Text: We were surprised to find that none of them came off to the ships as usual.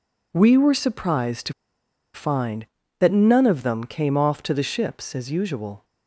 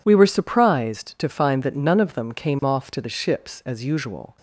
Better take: second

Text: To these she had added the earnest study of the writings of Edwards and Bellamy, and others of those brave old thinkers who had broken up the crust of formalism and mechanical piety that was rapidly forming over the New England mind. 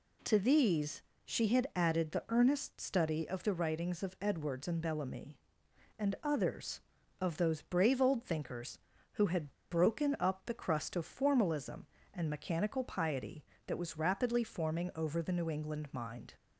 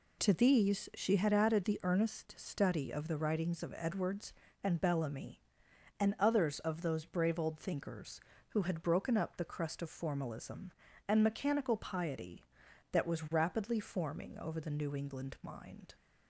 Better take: second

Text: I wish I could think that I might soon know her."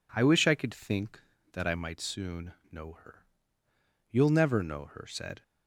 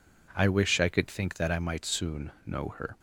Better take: second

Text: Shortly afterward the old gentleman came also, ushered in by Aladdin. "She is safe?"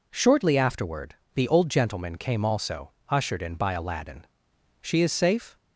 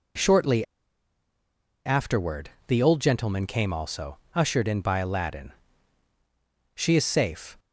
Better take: first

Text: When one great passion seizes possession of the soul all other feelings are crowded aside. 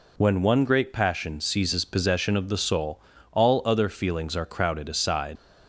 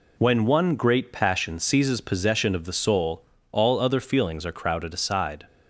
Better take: second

